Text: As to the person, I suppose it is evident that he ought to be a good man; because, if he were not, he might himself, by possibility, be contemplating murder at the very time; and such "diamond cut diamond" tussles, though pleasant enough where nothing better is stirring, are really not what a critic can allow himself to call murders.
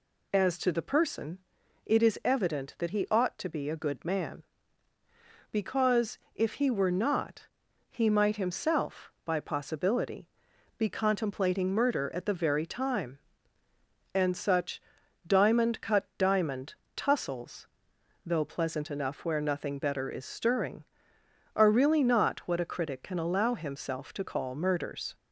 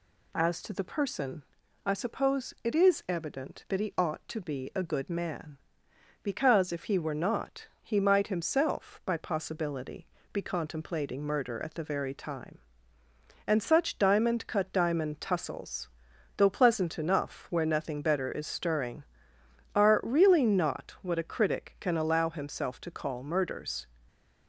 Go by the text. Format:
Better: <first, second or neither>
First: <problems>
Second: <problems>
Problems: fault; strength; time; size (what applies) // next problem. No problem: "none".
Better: second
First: skips "I suppose"; at 1.6 s // pauses between "such" and "diamond"; at 14.8 s; 0.44 s long // pauses between "diamond" and "tussles"; slight; at 16.7 s; 0.22 s long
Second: none